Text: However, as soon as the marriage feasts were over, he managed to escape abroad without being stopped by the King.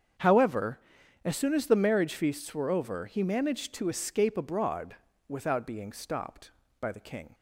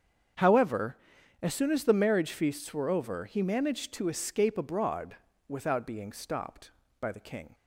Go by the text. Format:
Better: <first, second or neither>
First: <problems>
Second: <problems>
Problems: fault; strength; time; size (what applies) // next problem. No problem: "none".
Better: neither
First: starts louder than the rest; strong; until 1.6 s; 7.5 dB // pauses between "abroad" and "without"; slight; at 4.9 s; 0.34 s long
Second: starts louder than the rest; strong; until 1.8 s; 7.5 dB // pauses between "abroad" and "without"; slight; at 5.1 s; 0.33 s long